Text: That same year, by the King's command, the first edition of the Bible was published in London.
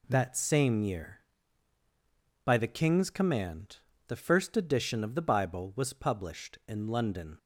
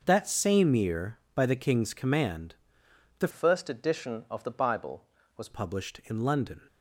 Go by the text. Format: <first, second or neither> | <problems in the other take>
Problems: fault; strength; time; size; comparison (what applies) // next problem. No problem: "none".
first | starts louder than the rest; noticeable; until 1.0 s; 6 dB // changes voice from "first" to "was"; from 3.3 to 5.4 s; 2.1 s long